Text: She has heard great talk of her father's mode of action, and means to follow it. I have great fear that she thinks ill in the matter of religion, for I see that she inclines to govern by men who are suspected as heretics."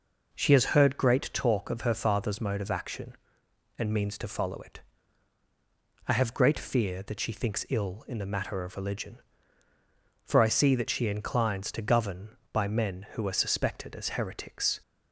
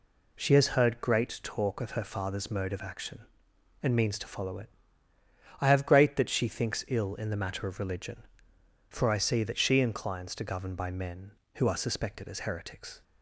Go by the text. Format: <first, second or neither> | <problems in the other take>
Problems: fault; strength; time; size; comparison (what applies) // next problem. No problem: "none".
first | skips "fear"; at 6.1 s